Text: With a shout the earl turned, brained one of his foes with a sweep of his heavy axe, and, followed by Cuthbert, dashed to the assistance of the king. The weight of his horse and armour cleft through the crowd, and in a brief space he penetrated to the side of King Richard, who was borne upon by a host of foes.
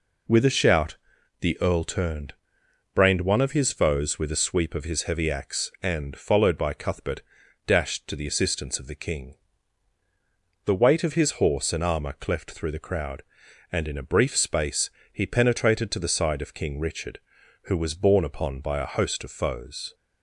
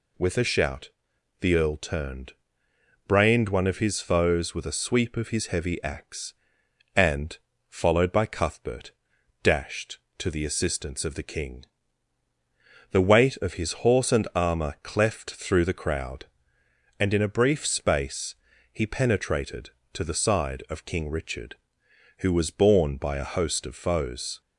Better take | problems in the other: first | pauses between "shout" and "the"; noticeable; at 0.9 s; 0.50 s long; also in the first // pauses between "space" and "he"; slight; at 18.3 s; 0.36 s long; slight in the first // skips "upon"; at 22.9 s

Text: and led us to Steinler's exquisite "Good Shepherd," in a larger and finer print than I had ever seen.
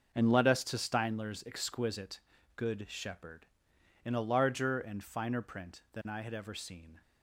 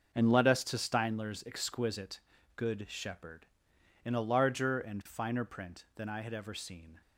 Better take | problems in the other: neither | starts louder than the rest; noticeable; the same in both // pauses between "exquisite" and "Good"; slight; the same in both

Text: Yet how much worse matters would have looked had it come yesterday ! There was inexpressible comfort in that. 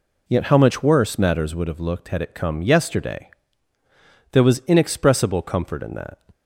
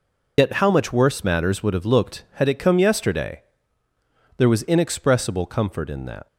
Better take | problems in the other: first | loses the start of "Yet"; at 0.3 s; 85 ms

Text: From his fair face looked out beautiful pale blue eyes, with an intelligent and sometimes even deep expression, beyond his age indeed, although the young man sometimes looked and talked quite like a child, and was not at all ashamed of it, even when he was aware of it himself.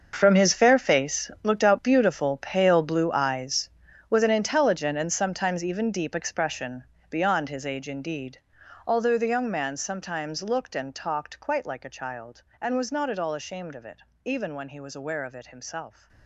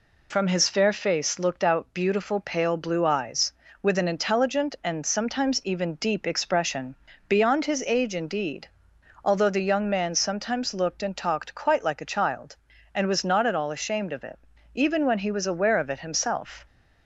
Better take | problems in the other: second | gets quieter; strong; throughout; 15 dB

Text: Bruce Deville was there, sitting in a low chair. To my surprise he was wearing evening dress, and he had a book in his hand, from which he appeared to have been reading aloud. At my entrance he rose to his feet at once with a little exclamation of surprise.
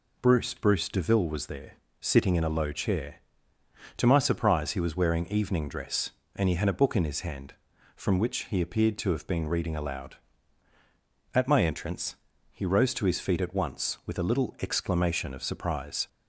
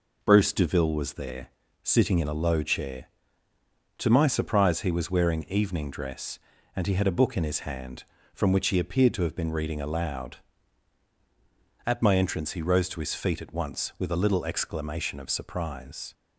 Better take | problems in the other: second | says "Bruce" twice; at 0.5 s // pauses between "entrance" and "he"; slight; at 12.1 s; 0.34 s long

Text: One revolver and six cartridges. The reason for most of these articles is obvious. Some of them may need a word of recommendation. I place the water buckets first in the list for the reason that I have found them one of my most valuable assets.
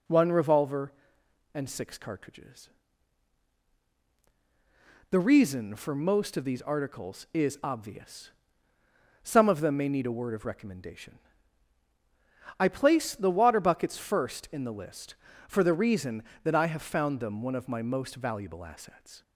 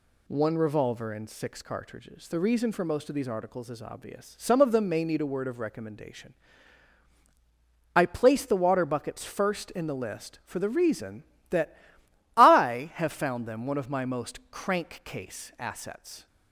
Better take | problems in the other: first | pauses between "that" and "I"; noticeable; at 11.7 s; 0.60 s long // says "crankcase" for "valuable"; at 14.5 s

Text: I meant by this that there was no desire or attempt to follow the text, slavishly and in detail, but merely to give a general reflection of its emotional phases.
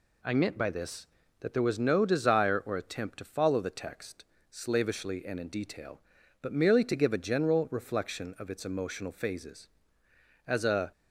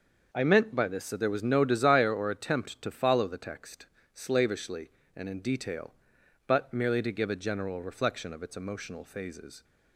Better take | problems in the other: second | goes on to say "As a"; slight; from 10.4 s on; 0.44 s long

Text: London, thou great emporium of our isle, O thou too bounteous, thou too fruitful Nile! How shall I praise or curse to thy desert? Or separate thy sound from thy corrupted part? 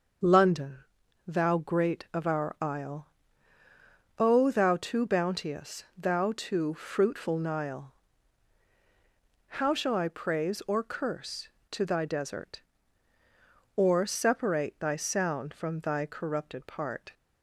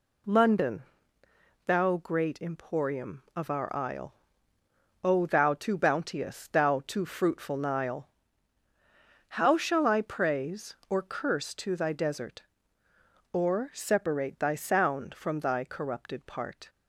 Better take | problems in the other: second | starts louder than the rest; noticeable; until 1.7 s; 6 dB // skips "emporium"; at 2.1 s

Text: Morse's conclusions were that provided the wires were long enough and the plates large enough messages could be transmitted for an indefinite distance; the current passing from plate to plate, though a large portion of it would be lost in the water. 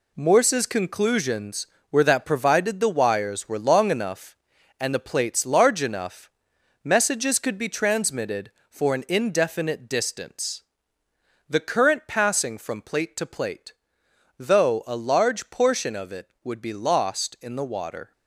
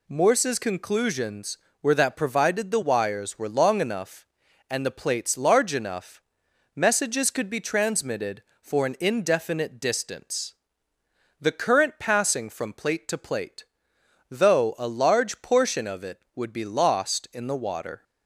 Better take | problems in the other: second | gets quieter; strong; throughout; 7.5 dB // pauses between "enough" and "messages"; noticeable; at 6.2 s; 0.54 s long; noticeable in the second

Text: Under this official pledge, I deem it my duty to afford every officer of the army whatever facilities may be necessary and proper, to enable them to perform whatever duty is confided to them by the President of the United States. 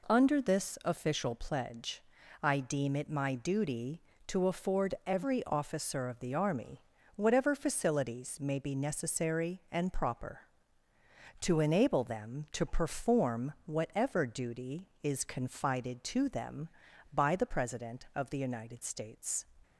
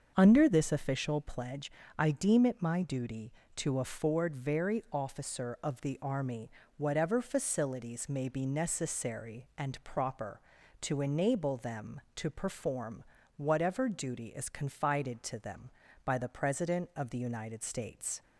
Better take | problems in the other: first | starts louder than the rest; until 1.1 s; 6.5 dB // says "very" for "every"; at 4.3 s // pauses between "army" and "whatever"; slight; at 6.4 s; 0.28 s long; slight in the first // pauses between "perform" and "whatever"; slight; at 13.0 s; 0.32 s long

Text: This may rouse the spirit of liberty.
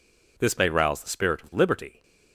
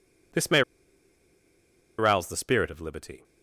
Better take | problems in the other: first | pauses between "may" and "rouse"; strong; at 0.6 s; 1.3 s long

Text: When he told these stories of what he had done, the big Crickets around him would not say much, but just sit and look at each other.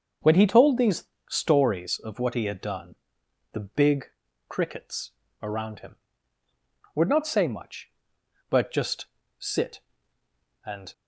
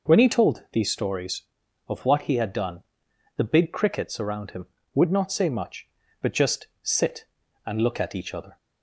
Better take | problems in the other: second | starts louder than the rest; until 1.4 s; 6.5 dB // pauses between "these" and "stories"; slight; at 1.0 s; 0.24 s long // pauses between "big" and "Crickets"; at 4.0 s; 0.42 s long // pauses between "Crickets" and "around"; slight; at 5.1 s; 0.28 s long // pauses between "just" and "sit"; slight; at 9.0 s; 0.32 s long // stops before "look at each other"; at 10.9 s

